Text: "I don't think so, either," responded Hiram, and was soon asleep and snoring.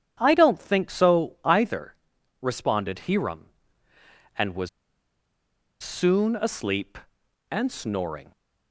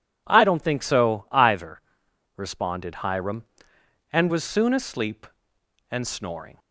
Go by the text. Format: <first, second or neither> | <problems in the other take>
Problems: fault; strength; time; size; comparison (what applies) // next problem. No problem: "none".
second | pauses between "was" and "soon"; at 4.6 s; 1.1 s long